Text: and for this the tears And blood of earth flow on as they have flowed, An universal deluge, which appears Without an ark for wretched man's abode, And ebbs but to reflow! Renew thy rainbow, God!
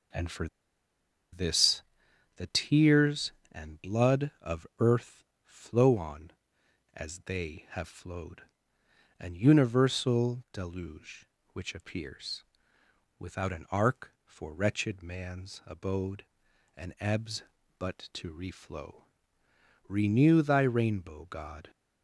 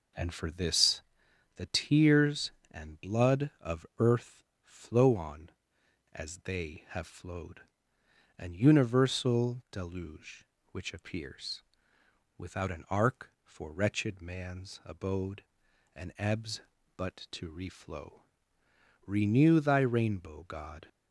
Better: second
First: pauses between "for" and "this"; noticeable; at 0.4 s; 0.85 s long // pauses between "this" and "the"; noticeable; at 1.8 s; 0.54 s long // pauses between "earth" and "flow"; slight; at 5.2 s; 0.20 s long // pauses between "appears" and "Without"; noticeable; at 12.4 s; 0.74 s long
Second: pauses between "this" and "the"; noticeable; at 1.0 s; 0.54 s long // pauses between "earth" and "flow"; slight; at 4.4 s; 0.19 s long // pauses between "appears" and "Without"; noticeable; at 11.6 s; 0.74 s long

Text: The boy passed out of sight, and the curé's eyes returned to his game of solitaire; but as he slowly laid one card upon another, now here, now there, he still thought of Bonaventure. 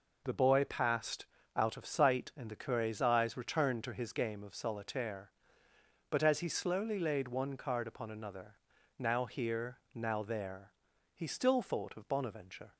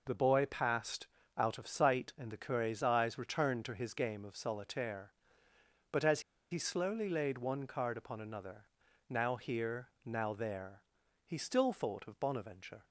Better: first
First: pauses between "passed" and "out"; slight; at 1.2 s; 0.30 s long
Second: pauses between "passed" and "out"; slight; at 1.0 s; 0.30 s long // pauses between "as" and "he"; slight; at 6.1 s; 0.31 s long

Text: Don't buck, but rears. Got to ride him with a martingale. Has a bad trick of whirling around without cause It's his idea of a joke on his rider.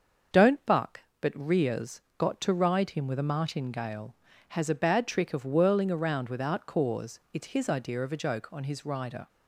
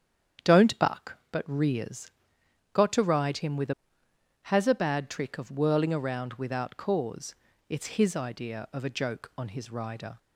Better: first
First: starts louder than the rest; until 1.6 s; 6.5 dB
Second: starts louder than the rest; strong; until 1.6 s; 8.5 dB // skips "martingale"; at 4.0 s // pauses between "cause" and "It's"; slight; at 7.3 s; 0.34 s long

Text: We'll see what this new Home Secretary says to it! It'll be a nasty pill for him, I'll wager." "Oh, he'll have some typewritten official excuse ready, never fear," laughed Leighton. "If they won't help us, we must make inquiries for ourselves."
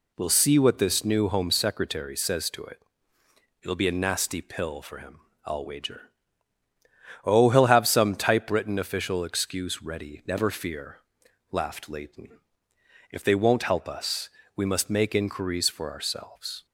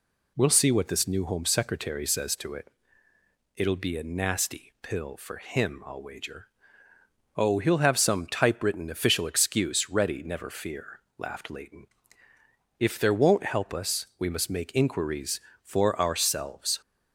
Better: first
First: none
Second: says "there" for "they"; at 12.9 s

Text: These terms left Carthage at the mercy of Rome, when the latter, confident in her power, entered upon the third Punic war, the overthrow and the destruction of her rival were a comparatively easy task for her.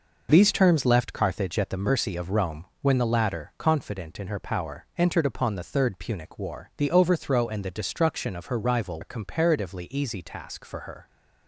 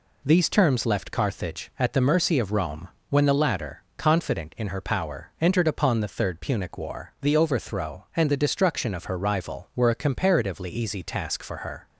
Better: second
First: skips "were"; at 9.0 s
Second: none

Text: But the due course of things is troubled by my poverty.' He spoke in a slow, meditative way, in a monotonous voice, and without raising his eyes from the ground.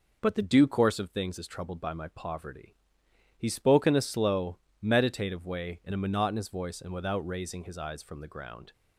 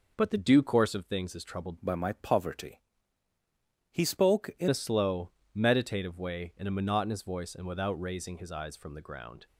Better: first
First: none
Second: changes voice from "by" to "in"; from 1.8 to 4.6 s; 2.8 s long

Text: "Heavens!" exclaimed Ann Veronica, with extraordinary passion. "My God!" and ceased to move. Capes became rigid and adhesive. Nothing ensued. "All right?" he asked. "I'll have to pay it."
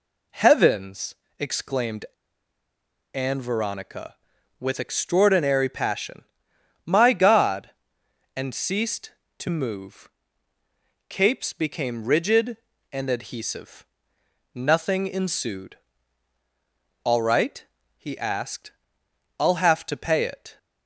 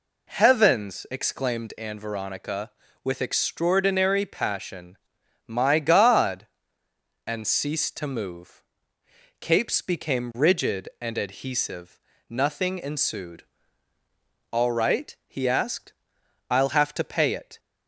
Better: second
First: pauses between "exclaimed" and "Ann"; at 2.0 s; 1.0 s long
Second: none

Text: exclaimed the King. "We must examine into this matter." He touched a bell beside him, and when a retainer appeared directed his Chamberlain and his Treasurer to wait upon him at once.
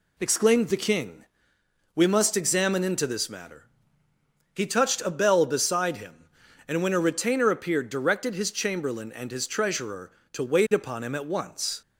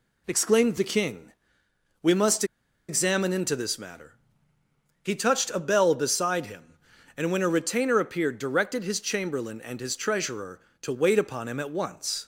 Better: first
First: none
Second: pauses between "must" and "examine"; at 2.4 s; 0.44 s long

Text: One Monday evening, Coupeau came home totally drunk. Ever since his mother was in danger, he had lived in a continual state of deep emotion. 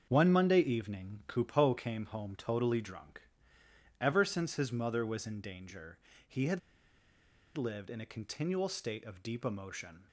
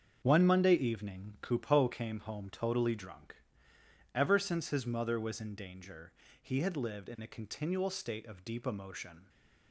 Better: second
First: starts louder than the rest; until 1.1 s; 7 dB // pauses between "had" and "lived"; noticeable; at 6.5 s; 0.97 s long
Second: starts louder than the rest; until 1.2 s; 7 dB

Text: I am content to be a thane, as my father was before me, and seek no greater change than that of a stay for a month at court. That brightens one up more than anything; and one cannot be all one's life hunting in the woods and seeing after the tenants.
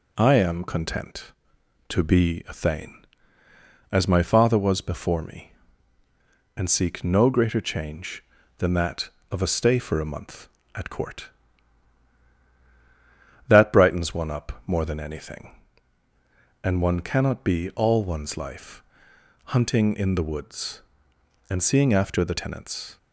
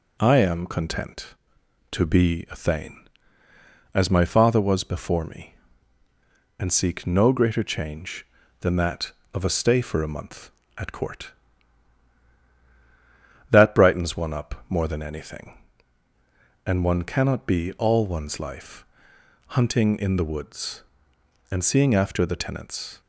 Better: neither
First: pauses between "life" and "hunting"; noticeable; at 18.8 s; 0.62 s long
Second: pauses between "life" and "hunting"; noticeable; at 18.8 s; 0.62 s long

